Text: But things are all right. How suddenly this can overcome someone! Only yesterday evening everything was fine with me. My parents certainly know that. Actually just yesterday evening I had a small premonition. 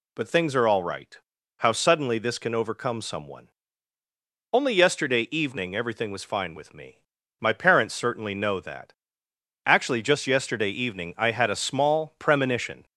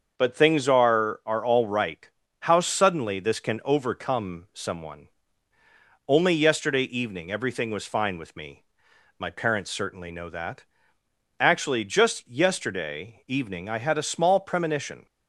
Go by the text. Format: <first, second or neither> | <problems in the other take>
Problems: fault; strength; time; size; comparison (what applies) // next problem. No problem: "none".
first | starts louder than the rest; until 1.1 s; 6.5 dB // says "are" twice; at 1.2 s